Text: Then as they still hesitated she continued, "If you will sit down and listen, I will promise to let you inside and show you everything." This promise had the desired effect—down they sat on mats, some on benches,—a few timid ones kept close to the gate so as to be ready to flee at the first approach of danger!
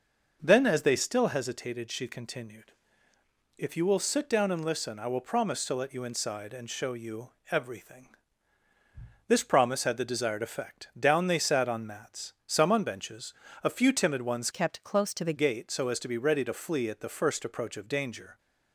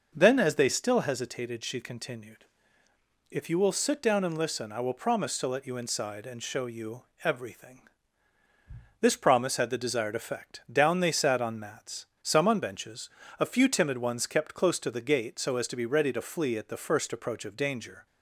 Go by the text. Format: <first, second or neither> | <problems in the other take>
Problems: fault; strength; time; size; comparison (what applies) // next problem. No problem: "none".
second | pauses between "you" and "everything"; slight; at 7.3 s; 0.20 s long; slight in the second // changes voice from "kept" to "the"; from 14.5 to 15.3 s; 0.8 s long